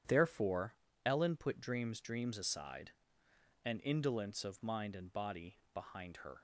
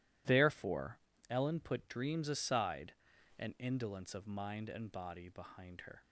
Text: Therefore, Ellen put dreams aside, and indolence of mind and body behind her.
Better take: second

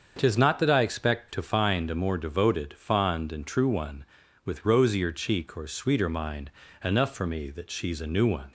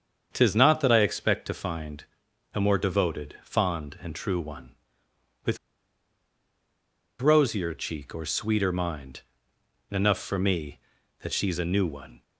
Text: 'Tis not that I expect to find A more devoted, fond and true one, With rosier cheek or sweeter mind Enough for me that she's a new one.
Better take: first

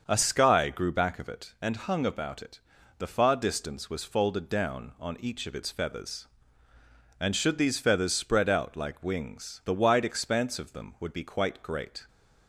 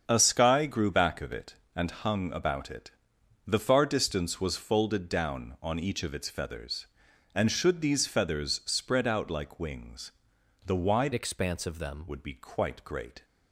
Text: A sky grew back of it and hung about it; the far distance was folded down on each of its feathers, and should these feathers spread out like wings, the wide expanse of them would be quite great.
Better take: first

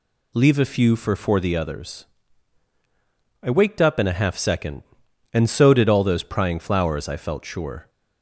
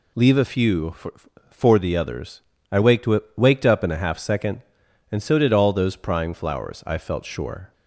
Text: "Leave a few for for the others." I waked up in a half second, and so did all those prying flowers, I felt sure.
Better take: first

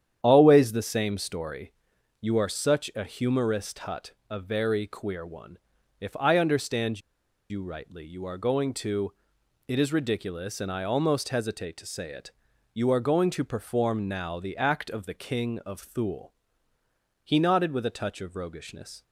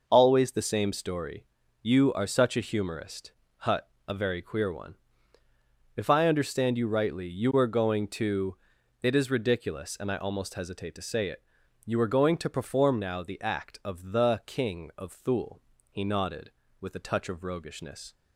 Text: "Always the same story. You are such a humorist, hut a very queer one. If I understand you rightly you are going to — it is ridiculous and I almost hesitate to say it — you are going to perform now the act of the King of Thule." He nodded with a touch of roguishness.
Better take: second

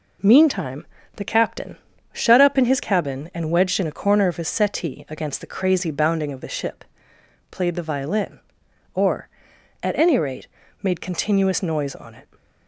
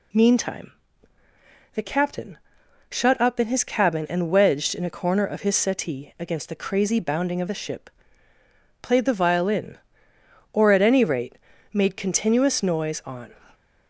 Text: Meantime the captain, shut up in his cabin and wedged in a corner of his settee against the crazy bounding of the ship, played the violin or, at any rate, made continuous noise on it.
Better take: first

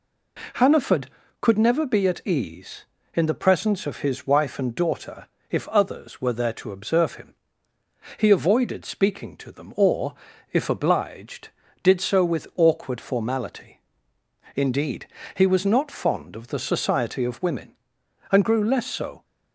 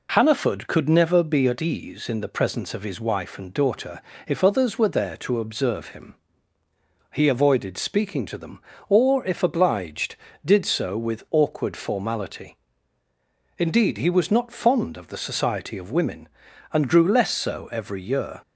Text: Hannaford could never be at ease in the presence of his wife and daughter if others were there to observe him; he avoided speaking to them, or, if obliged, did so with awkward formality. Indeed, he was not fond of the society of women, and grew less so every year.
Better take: second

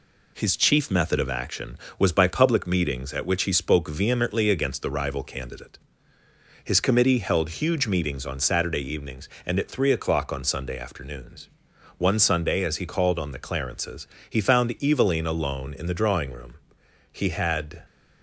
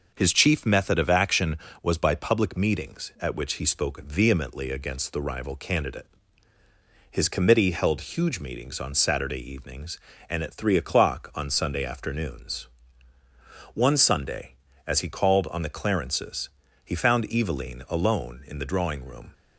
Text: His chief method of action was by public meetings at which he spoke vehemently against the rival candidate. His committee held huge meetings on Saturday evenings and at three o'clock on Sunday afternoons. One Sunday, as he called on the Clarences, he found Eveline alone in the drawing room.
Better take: second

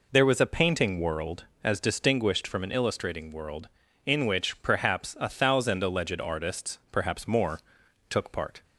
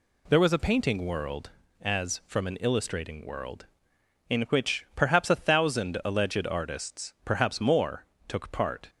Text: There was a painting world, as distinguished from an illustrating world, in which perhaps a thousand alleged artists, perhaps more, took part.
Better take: first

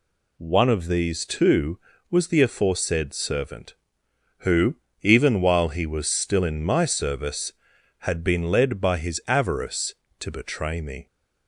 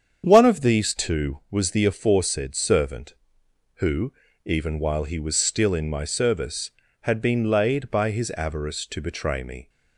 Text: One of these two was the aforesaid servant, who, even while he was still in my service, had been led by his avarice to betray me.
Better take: first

